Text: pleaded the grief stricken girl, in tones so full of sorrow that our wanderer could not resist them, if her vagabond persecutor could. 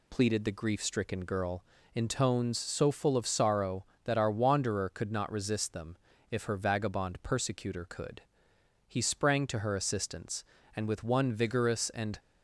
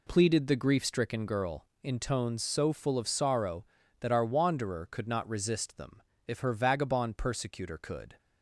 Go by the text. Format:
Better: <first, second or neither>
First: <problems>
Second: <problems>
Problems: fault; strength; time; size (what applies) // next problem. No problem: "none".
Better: second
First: goes on to say "He sprang to her assistance and with one vigorous and"; strong; from 8.8 s on; 3.3 s long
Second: none